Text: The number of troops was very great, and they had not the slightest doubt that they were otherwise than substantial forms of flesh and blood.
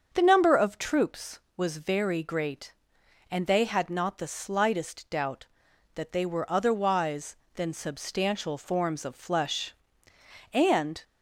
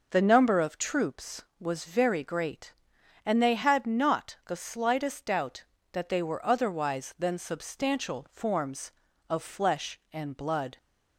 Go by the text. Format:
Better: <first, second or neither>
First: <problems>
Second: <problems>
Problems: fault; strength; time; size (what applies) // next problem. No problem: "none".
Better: second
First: starts louder than the rest; until 1.1 s; 7 dB // stops before "blood"; at 11.0 s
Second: none